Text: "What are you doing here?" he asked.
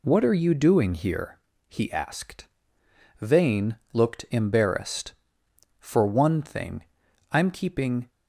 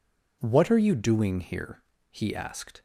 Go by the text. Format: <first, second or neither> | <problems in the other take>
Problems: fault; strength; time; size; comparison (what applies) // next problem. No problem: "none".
second | goes on to say "Vane looked embarrassed For one thing I'm keeping"; strong; from 3.2 s on; 4.8 s long